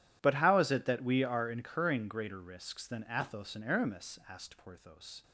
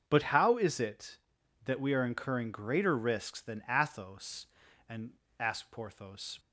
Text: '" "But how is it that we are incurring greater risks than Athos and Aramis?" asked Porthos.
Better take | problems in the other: first | starts louder than the rest; until 1.0 s; 7 dB // skips "Aramis"; at 5.2 s

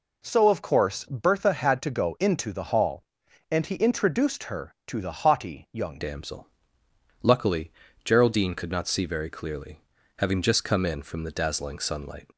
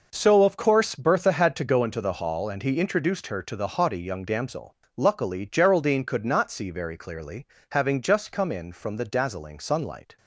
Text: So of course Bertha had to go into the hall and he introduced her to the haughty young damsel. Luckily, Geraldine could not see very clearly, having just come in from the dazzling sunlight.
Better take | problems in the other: second | changes voice at "damsel"; from 5.9 s on; 6.3 s long

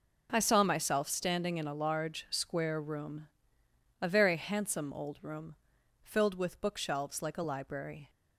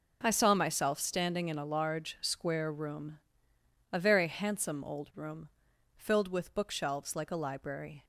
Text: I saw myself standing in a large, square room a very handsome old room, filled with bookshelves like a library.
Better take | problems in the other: neither | pauses between "room" and "a"; noticeable; the same in both

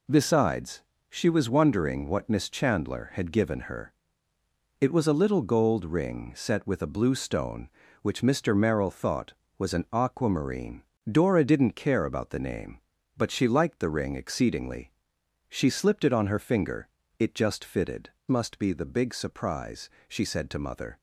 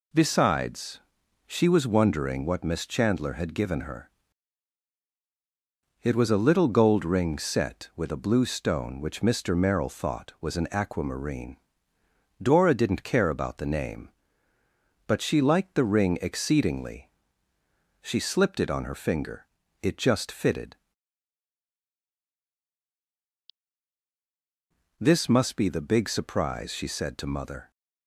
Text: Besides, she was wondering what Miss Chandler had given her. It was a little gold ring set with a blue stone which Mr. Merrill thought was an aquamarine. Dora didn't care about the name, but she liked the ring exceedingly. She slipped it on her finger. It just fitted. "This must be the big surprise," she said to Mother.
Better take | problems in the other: second | skips "This"; at 18.2 s

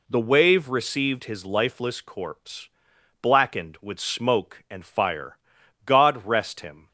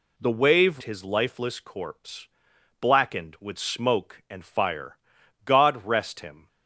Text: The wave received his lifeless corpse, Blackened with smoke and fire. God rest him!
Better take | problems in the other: first | skips "received"; at 0.8 s

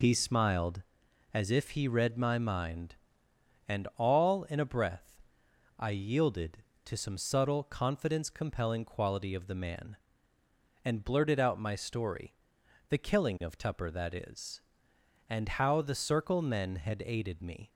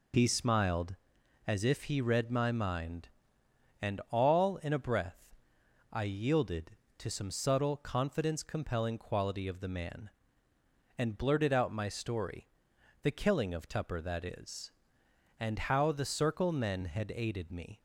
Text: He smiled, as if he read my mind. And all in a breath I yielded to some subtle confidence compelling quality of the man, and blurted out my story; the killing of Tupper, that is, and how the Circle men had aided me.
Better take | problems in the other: neither | pauses between "breath" and "I"; noticeable; the same in both

